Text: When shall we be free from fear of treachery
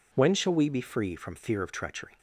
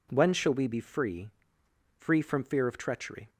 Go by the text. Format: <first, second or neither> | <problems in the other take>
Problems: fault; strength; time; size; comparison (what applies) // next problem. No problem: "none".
first | says "free" twice; at 1.9 s